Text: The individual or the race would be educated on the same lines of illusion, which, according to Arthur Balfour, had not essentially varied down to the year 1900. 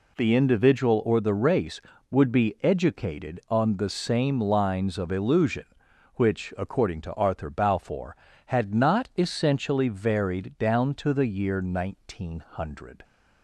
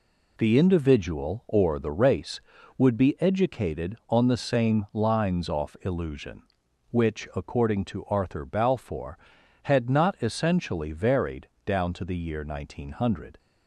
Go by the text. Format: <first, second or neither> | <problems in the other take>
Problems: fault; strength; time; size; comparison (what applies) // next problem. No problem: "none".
first | says "off" for "of"; at 5.4 s // pauses between "varied" and "down"; slight; at 11.4 s; 0.18 s long